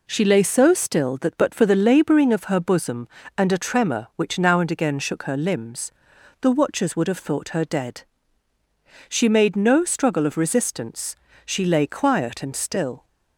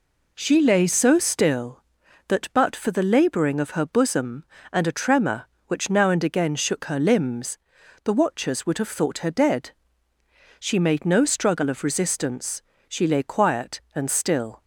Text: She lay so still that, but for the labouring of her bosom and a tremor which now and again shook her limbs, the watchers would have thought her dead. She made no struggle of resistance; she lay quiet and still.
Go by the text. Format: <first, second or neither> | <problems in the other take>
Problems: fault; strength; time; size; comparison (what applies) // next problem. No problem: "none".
neither | none